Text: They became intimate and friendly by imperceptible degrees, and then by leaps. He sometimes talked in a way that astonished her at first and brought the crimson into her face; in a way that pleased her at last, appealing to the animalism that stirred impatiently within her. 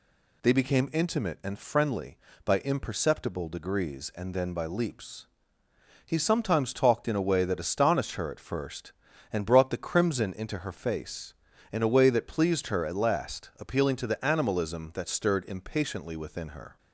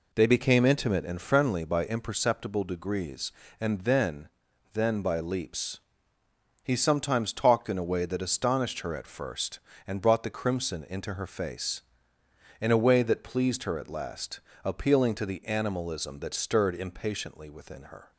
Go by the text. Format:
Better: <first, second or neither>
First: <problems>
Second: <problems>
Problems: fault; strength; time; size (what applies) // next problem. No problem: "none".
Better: first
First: none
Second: says "then" twice; at 4.7 s